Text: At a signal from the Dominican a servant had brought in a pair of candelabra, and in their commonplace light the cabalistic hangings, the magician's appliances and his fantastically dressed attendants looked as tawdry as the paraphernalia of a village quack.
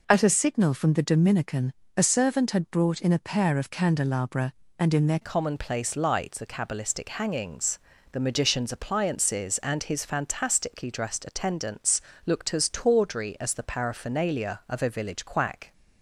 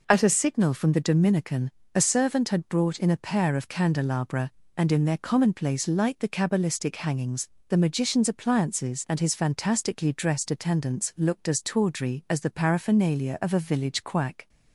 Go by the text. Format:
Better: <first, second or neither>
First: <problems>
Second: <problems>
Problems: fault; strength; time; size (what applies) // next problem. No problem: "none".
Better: second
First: pauses between "Dominican" and "a"; slight; at 1.7 s; 0.24 s long // changes voice at "commonplace"; from 5.2 s on; 10.5 s long // pauses between "attendants" and "looked"; slight; at 12.0 s; 0.24 s long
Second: pauses between "Dominican" and "a"; slight; at 1.7 s; 0.24 s long